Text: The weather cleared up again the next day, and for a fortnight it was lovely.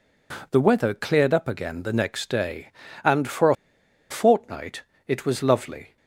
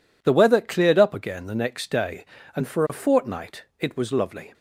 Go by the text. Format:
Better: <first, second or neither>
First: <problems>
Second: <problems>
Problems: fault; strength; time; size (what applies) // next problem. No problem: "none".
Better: second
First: pauses between "a" and "fortnight"; noticeable; at 3.5 s; 0.55 s long // pauses between "fortnight" and "it"; slight; at 4.8 s; 0.26 s long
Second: none